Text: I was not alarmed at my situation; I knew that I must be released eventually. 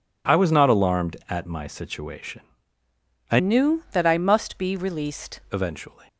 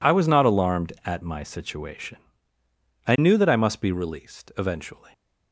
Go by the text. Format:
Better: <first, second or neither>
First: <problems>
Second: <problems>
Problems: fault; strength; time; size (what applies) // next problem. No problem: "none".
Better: second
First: changes voice from "knew" to "released"; from 3.3 to 5.3 s; 2.0 s long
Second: none